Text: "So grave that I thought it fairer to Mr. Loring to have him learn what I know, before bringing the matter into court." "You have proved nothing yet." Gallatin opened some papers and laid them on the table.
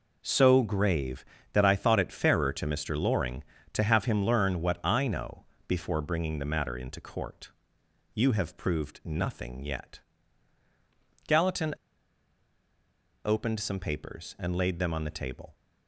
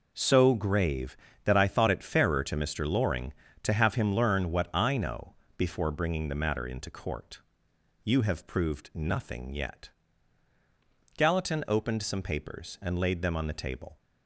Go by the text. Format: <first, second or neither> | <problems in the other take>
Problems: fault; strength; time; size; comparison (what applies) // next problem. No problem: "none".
second | pauses between "Gallatin" and "opened"; strong; at 11.7 s; 1.5 s long